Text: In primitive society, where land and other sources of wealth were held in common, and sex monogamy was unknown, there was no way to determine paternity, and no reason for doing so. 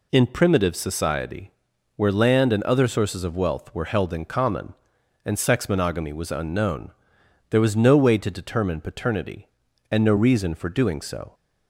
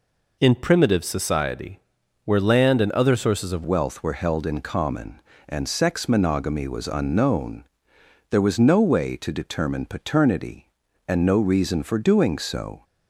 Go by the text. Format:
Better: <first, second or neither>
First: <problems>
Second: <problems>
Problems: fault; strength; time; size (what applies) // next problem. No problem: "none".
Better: first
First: none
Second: changes voice at "wealth"; from 3.6 s on; 9.2 s long